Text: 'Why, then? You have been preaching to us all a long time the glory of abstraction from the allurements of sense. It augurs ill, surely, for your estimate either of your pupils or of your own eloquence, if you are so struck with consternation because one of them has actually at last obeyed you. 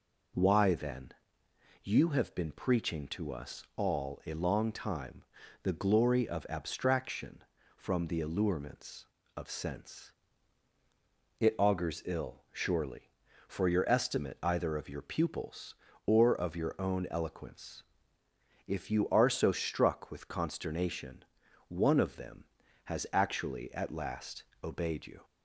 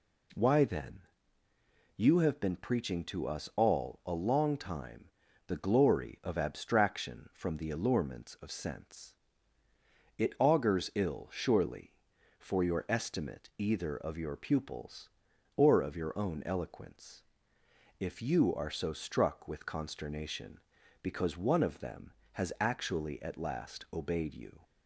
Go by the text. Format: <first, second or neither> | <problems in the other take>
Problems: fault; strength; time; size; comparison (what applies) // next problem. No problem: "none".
second | pauses between "time" and "the"; at 5.2 s; 0.40 s long; also in the second // skips "because"; at 21.4 s // pauses between "last" and "obeyed"; slight; at 24.4 s; 0.22 s long